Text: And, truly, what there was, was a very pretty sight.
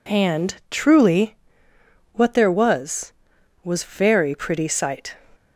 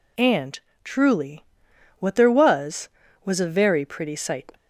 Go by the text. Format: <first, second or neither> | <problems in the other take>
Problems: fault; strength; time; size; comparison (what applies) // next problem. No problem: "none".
second | skips "a"; at 3.8 s